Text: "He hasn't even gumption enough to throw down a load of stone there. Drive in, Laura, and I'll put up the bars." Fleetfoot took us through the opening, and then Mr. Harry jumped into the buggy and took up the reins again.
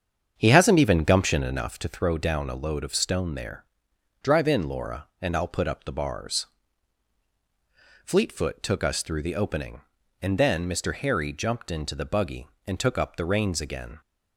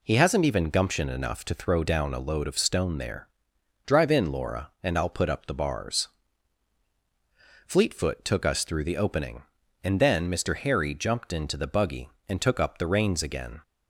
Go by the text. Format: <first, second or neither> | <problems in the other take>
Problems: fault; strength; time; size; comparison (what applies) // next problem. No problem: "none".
second | starts louder than the rest; strong; until 1.7 s; 7.5 dB